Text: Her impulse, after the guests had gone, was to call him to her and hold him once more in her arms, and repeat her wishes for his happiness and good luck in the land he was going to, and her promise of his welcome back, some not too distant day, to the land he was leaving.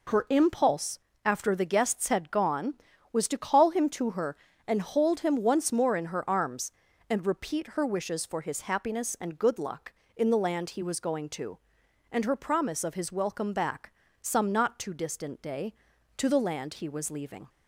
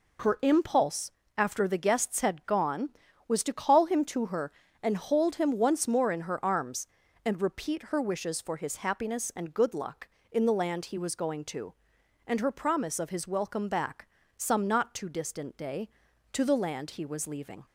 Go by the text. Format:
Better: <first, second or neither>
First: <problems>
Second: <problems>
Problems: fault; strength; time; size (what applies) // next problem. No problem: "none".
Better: neither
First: none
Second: none